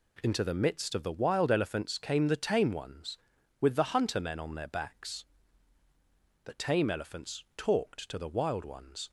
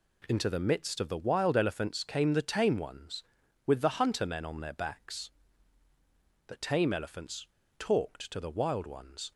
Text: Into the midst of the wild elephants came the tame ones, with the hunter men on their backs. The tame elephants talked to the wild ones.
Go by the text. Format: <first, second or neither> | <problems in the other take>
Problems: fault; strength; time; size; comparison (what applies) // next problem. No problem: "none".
first | pauses between "elephants" and "talked"; slight; at 7.4 s; 0.31 s long